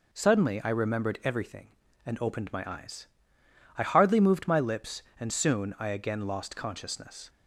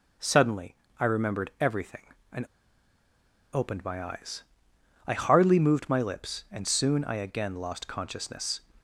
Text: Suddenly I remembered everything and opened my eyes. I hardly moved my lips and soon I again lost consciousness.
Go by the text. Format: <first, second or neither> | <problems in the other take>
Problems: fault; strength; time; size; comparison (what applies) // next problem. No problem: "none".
first | pauses between "Suddenly" and "I"; slight; at 0.7 s; 0.26 s long // pauses between "and" and "opened"; at 2.4 s; 1.0 s long